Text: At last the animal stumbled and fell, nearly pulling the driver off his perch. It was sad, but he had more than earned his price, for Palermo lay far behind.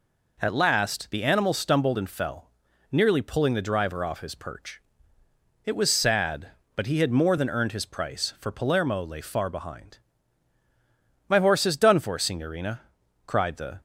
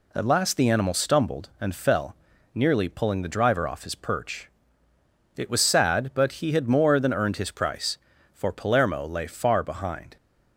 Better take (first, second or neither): second